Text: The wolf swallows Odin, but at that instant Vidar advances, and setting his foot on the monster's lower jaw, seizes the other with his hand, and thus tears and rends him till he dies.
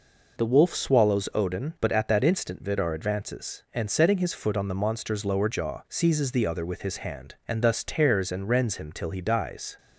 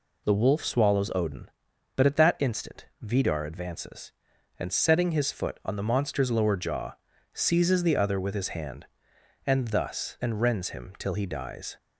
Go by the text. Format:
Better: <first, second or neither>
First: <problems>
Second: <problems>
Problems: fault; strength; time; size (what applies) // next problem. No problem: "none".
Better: first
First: none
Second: pauses between "instant" and "Vidar"; slight; at 2.8 s; 0.16 s long // skips "tears"; at 10.1 s